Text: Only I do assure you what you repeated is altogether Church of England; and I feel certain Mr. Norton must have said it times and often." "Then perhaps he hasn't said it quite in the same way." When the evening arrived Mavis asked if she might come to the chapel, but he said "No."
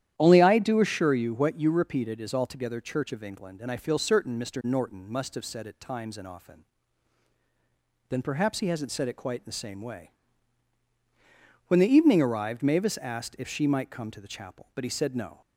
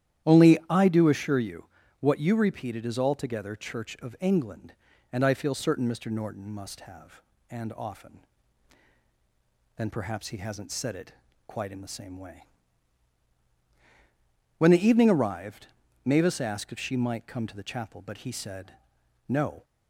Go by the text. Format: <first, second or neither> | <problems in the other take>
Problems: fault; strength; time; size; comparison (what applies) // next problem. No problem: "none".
first | starts louder than the rest; strong; until 1.3 s; 11.5 dB; strong in the first // pauses between "you" and "what"; slight; at 1.6 s; 0.34 s long // skips "said it times"; at 7.3 s // pauses between "it" and "quite"; slight; at 11.1 s; 0.34 s long // pauses between "arrived" and "Mavis"; at 15.6 s; 0.38 s long // pauses between "said" and "No"; noticeable; at 18.7 s; 0.52 s long